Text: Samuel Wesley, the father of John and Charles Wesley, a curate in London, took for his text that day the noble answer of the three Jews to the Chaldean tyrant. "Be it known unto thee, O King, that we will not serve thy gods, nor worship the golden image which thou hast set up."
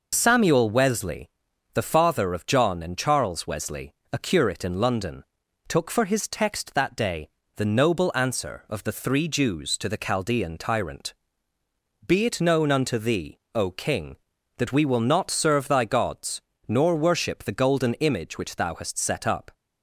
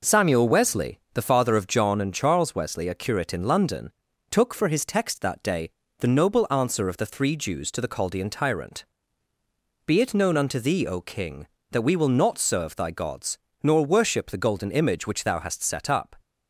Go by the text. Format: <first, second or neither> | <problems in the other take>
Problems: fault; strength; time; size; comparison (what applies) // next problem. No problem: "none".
second | loses the start of "Samuel"; at 0.1 s; 30 ms // pauses between "day" and "the"; slight; at 7.2 s; 0.26 s long; slight in the second